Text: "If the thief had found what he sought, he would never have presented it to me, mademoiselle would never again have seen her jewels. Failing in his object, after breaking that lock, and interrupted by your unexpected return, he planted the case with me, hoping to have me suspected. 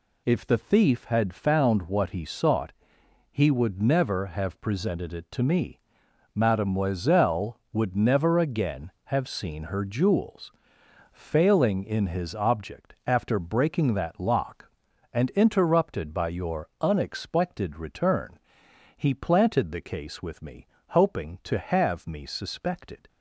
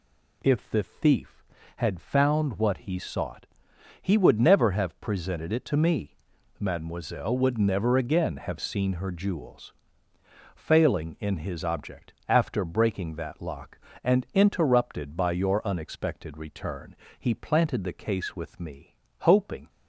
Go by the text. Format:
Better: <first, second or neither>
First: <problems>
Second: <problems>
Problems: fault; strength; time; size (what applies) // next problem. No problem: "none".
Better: first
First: none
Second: stops before "to have me suspected"; at 19.6 s